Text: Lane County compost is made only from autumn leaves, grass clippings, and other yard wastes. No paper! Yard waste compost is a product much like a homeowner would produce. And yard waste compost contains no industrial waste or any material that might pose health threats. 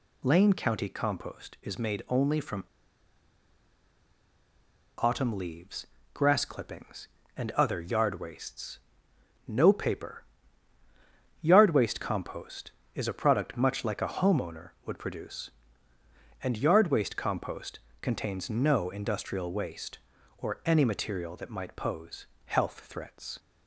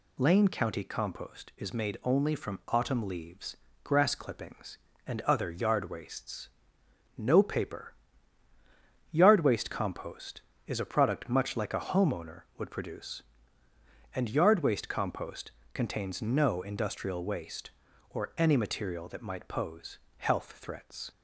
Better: second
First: pauses between "from" and "autumn"; strong; at 2.6 s; 2.3 s long // pauses between "compost" and "contains"; slight; at 17.7 s; 0.22 s long // pauses between "pose" and "health"; slight; at 22.2 s; 0.20 s long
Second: pauses between "compost" and "contains"; slight; at 15.5 s; 0.22 s long // pauses between "pose" and "health"; slight; at 19.9 s; 0.20 s long

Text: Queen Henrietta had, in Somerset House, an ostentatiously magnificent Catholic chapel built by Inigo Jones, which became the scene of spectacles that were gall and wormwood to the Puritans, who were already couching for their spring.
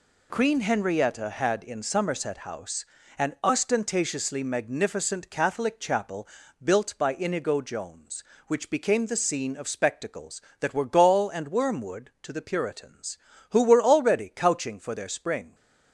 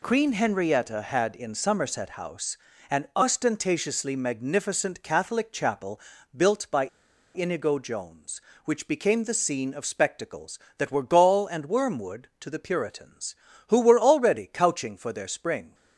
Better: first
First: pauses between "chapel" and "built"; at 6.2 s; 0.38 s long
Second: pauses between "chapel" and "built"; at 5.9 s; 0.38 s long // pauses between "by" and "Inigo"; noticeable; at 6.8 s; 0.47 s long

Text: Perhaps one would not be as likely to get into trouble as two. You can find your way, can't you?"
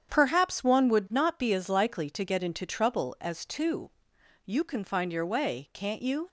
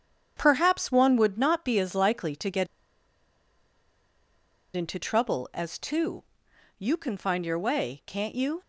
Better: first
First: starts louder than the rest; strong; until 1.1 s; 8.5 dB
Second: starts louder than the rest; strong; until 1.3 s; 8.5 dB // pauses between "get" and "into"; strong; at 2.6 s; 2.1 s long

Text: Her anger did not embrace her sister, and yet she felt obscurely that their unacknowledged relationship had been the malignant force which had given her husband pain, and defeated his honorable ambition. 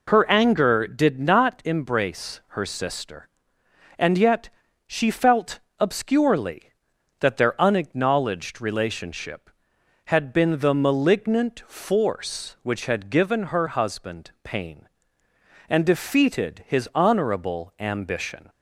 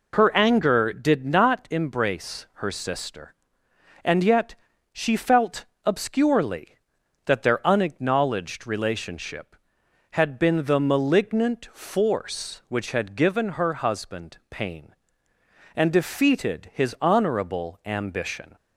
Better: neither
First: pauses between "yet" and "she"; at 4.4 s; 0.38 s long // pauses between "felt" and "obscurely"; slight; at 5.5 s; 0.20 s long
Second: pauses between "yet" and "she"; at 4.5 s; 0.38 s long // pauses between "felt" and "obscurely"; slight; at 5.6 s; 0.20 s long

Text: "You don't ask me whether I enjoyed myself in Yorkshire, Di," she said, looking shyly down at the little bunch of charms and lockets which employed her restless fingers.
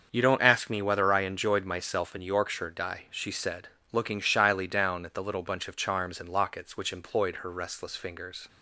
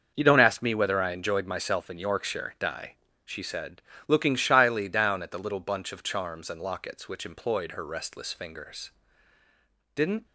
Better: first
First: starts louder than the rest; until 1.1 s; 6.5 dB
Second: starts louder than the rest; until 1.1 s; 6.5 dB // goes on to say "Didn't"; slight; from 9.9 s on; 0.30 s long

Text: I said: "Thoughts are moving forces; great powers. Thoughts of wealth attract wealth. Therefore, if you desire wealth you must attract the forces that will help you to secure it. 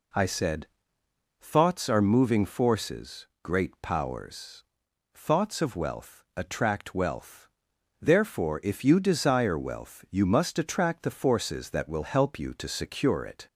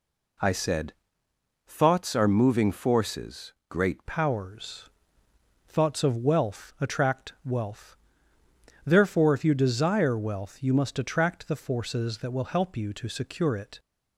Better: first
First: none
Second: changes voice at "powers"; from 4.0 s on; 9.7 s long

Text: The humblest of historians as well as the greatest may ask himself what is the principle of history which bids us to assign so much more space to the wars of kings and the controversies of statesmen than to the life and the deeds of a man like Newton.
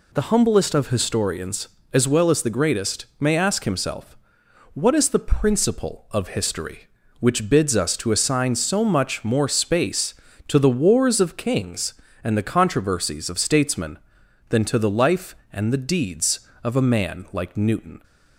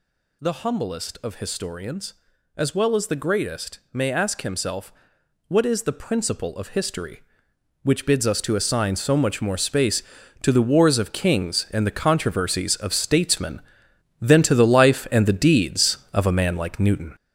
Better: first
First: pauses between "himself" and "what"; noticeable; at 4.1 s; 0.60 s long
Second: gets louder; throughout; 6.5 dB // pauses between "himself" and "what"; noticeable; at 4.9 s; 0.58 s long

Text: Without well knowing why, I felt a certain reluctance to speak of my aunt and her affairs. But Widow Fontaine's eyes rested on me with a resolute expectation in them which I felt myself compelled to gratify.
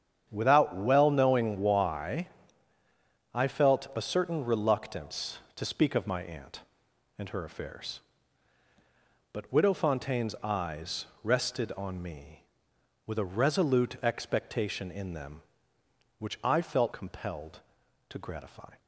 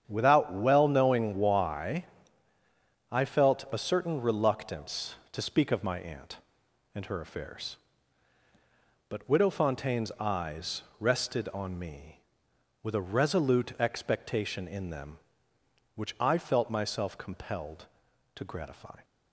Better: second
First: starts louder than the rest; strong; until 1.3 s; 8.5 dB // pauses between "eyes" and "rested"; slight; at 11.0 s; 0.18 s long // skips "myself"; at 16.9 s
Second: starts louder than the rest; strong; until 1.0 s; 8.5 dB // pauses between "eyes" and "rested"; slight; at 10.8 s; 0.18 s long

